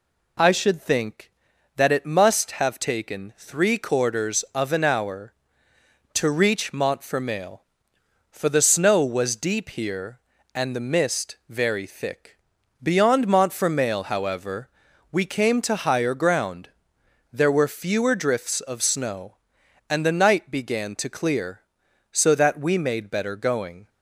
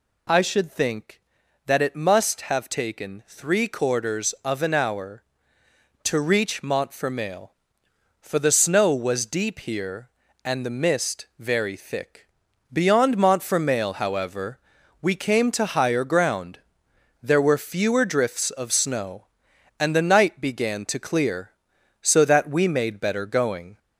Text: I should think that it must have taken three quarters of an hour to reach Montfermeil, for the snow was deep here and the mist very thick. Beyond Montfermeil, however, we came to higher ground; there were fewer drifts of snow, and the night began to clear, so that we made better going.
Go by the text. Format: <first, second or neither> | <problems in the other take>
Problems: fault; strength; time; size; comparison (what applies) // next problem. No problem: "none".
first | gets louder; slight; throughout; 2.5 dB